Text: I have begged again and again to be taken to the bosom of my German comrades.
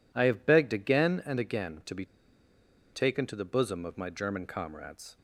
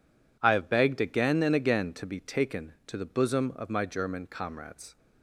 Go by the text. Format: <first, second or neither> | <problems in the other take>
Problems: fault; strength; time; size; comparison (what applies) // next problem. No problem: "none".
second | pauses between "be" and "taken"; noticeable; at 2.0 s; 0.88 s long